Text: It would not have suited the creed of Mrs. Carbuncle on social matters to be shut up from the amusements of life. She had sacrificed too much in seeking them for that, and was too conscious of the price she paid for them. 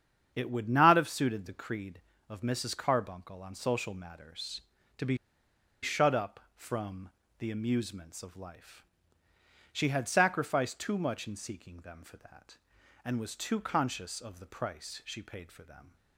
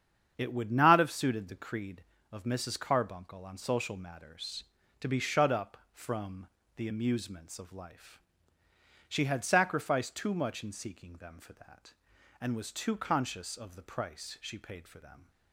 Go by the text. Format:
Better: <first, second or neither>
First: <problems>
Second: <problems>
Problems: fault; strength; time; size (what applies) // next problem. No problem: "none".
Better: second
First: starts louder than the rest; strong; until 1.3 s; 8 dB // pauses between "be" and "shut"; noticeable; at 5.1 s; 0.66 s long // pauses between "from" and "the"; slight; at 7.0 s; 0.30 s long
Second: starts louder than the rest; strong; until 1.3 s; 8 dB // pauses between "from" and "the"; slight; at 6.4 s; 0.30 s long